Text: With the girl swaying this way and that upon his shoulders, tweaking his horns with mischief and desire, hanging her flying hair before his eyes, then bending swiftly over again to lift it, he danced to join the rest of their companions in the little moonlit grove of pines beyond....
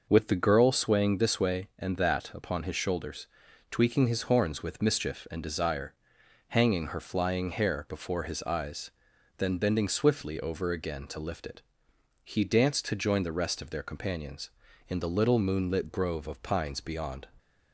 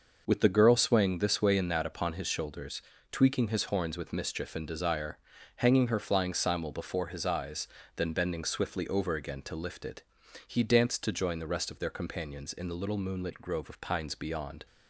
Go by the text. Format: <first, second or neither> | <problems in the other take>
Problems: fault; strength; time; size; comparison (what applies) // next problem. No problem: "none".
first | says "simul" for "hair"; at 6.3 s